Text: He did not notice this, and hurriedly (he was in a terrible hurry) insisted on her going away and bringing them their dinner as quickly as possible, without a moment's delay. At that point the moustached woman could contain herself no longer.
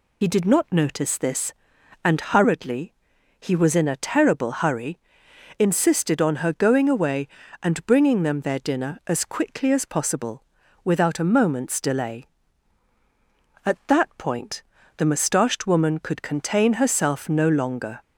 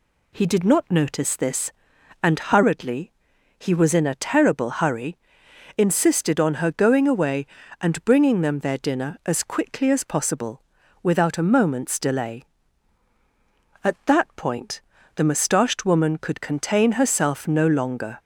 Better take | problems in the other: second | loses the start of "He"; at 0.2 s; 60 ms // pauses between "point" and "the"; slight; at 14.6 s; 0.32 s long; slight in the second

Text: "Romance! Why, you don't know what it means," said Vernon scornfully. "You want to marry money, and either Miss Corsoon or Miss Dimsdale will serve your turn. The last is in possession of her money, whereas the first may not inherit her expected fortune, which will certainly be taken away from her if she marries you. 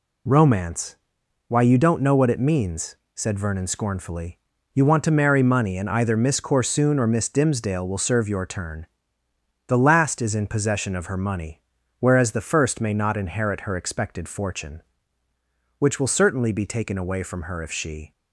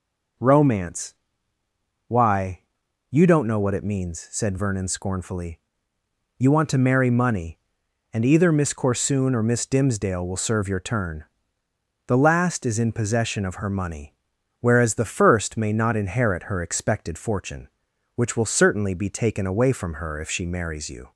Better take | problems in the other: second | stops before "marries you"; at 18.1 s

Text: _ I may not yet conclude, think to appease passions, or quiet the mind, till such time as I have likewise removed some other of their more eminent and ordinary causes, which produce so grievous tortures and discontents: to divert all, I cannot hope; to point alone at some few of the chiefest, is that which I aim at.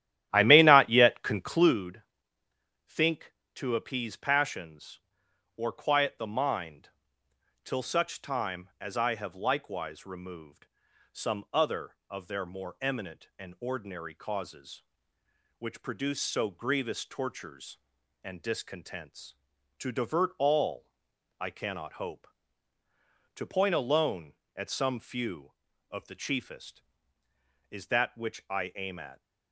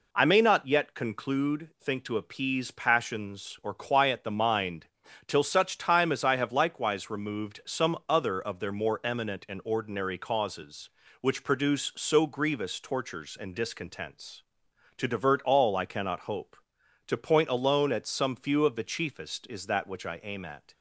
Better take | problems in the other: second | starts louder than the rest; strong; until 1.8 s; 13 dB // pauses between "removed" and "some"; noticeable; at 10.6 s; 0.46 s long

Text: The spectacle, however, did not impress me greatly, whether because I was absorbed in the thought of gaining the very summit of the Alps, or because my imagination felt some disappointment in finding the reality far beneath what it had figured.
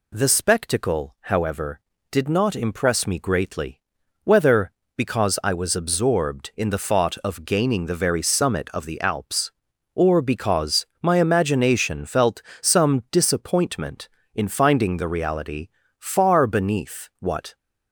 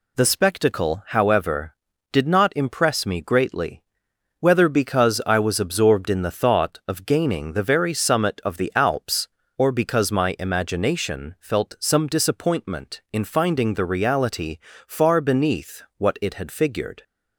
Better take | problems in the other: second | pauses between "because" and "my"; slight; at 10.8 s; 0.16 s long // pauses between "felt" and "some"; slight; at 12.4 s; 0.18 s long // pauses between "reality" and "far"; slight; at 15.6 s; 0.28 s long; slight in the second // stops before "it had figured"; at 17.5 s

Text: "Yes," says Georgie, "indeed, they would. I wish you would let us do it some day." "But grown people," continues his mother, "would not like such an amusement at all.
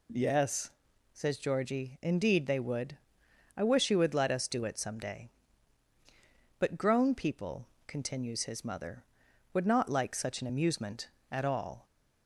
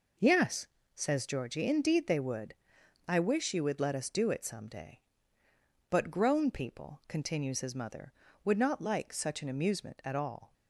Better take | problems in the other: neither | none

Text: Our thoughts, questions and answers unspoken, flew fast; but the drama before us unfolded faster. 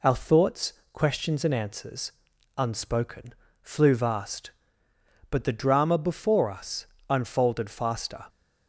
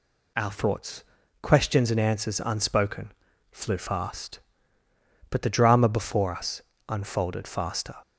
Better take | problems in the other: second | pauses between "answers" and "unspoken"; noticeable; at 2.1 s; 0.46 s long // says "vast" for "fast"; at 3.9 s // pauses between "us" and "unfolded"; slight; at 6.8 s; 0.24 s long; slight in the second

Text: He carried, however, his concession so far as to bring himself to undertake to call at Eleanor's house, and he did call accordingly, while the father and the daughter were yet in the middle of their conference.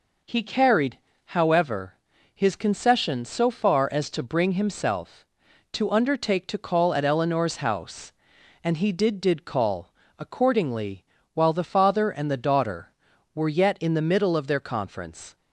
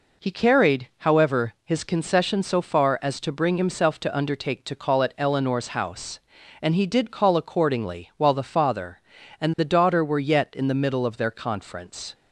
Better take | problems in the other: second | says "did" twice; at 9.1 s // pauses between "call" and "accordingly"; slight; at 9.9 s; 0.28 s long

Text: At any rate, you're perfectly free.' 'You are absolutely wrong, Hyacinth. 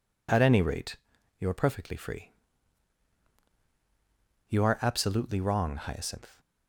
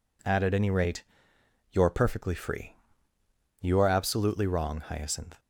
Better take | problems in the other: first | says "At" twice; at 0.4 s

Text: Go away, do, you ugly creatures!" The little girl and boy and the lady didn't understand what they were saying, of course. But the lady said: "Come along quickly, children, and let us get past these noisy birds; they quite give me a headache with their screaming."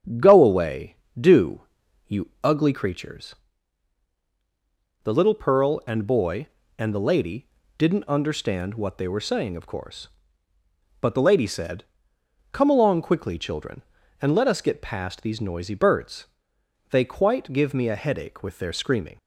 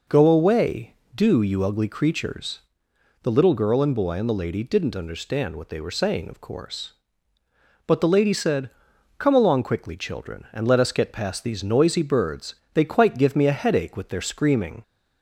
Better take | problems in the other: second | starts louder than the rest; strong; until 1.4 s; 8 dB // says "pearl" for "girl"; at 5.3 s // pauses between "lady" and "didn't"; slight; at 7.4 s; 0.32 s long

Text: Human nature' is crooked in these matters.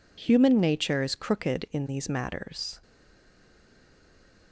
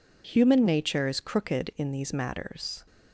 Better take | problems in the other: second | stays silent after the last word; noticeable; from 2.8 s on; 1.7 s long

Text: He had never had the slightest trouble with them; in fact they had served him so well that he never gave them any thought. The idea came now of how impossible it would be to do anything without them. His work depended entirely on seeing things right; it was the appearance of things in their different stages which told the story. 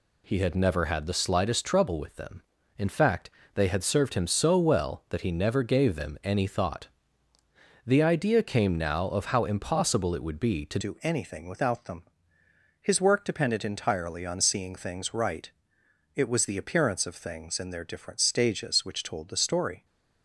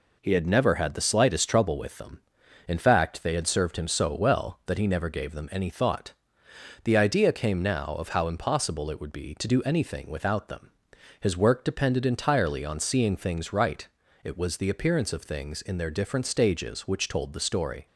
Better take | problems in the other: second | pauses between "fact" and "they"; slight; at 3.2 s; 0.24 s long // changes voice at "do"; from 10.8 s on; 9.0 s long

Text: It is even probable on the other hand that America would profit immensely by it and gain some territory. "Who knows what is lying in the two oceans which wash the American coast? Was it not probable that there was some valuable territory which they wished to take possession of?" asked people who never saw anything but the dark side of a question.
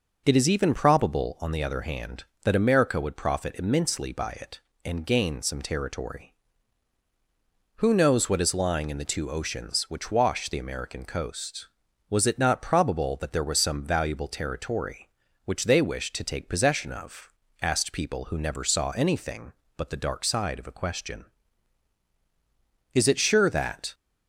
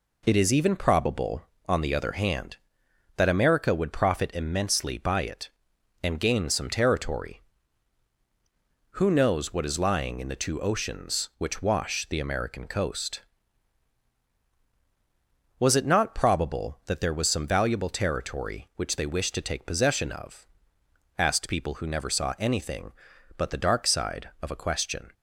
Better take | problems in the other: second | goes on to say "Is it sure that"; noticeable; from 22.9 s on; 1.0 s long

